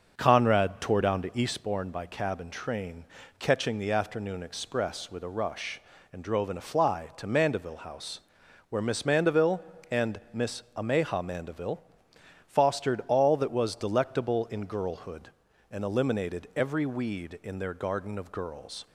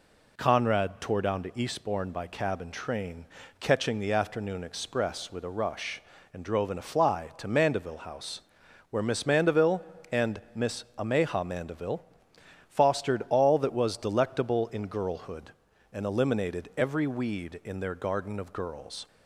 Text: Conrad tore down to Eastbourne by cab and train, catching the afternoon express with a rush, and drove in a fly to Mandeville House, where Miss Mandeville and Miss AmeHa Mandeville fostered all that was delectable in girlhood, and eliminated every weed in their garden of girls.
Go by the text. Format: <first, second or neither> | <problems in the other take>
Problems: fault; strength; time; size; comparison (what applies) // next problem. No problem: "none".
second | starts louder than the rest; until 1.8 s; 6 dB // pauses between "Mandeville" and "fostered"; noticeable; at 11.8 s; 0.64 s long; noticeable in the second